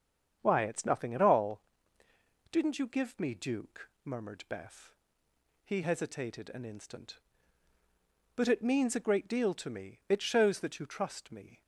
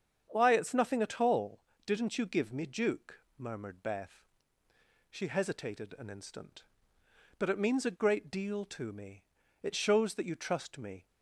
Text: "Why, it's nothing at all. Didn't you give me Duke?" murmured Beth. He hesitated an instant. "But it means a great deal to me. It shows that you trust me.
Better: first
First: starts louder than the rest; strong; until 1.4 s; 7.5 dB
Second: starts louder than the rest; strong; until 1.3 s; 7.5 dB // says "She" for "He"; at 5.0 s

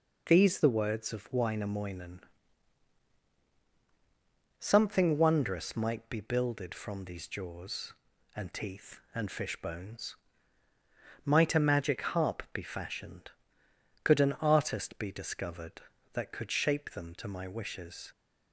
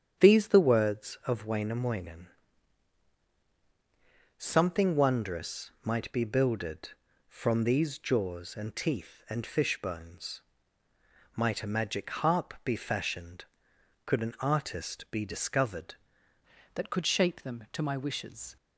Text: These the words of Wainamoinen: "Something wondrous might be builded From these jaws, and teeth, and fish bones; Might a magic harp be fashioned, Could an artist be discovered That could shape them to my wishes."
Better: first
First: none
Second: starts louder than the rest; strong; until 1.2 s; 8.5 dB // changes voice at "That"; from 16.7 s on; 1.8 s long

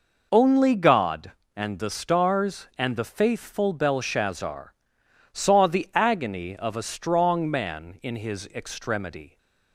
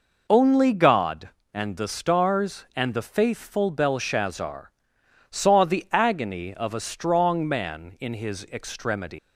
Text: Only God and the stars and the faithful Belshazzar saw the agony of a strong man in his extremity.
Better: first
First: pauses between "Belshazzar" and "saw"; noticeable; at 4.7 s; 0.58 s long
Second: pauses between "Belshazzar" and "saw"; noticeable; at 4.7 s; 0.58 s long // leaves "extremity" unfinished; at 9.1 s; 160 ms

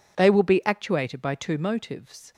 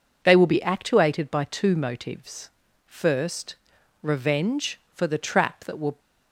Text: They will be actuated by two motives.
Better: first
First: none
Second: goes on to say "First revenge for the trap that will"; strong; from 2.8 s on; 3.1 s long

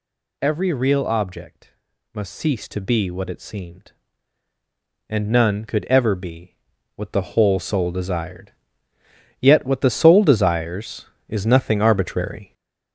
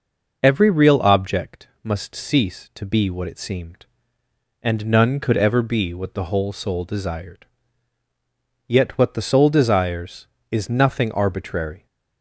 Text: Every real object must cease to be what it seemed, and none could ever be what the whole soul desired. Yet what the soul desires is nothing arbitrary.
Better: second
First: gets louder; throughout; 7 dB // pauses between "object" and "must"; at 1.7 s; 0.40 s long // pauses between "be" and "what"; at 6.5 s; 0.42 s long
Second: pauses between "object" and "must"; slight; at 1.6 s; 0.16 s long

